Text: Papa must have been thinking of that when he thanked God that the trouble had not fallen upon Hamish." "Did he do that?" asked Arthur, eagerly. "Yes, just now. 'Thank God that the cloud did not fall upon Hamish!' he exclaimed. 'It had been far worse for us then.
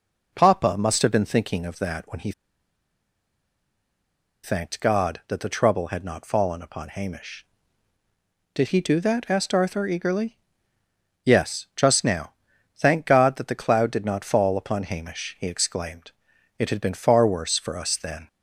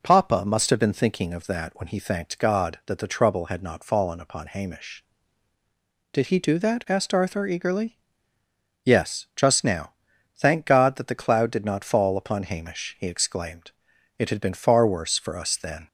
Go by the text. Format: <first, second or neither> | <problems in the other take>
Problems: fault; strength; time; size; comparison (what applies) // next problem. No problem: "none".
second | pauses between "he" and "thanked"; strong; at 2.3 s; 2.1 s long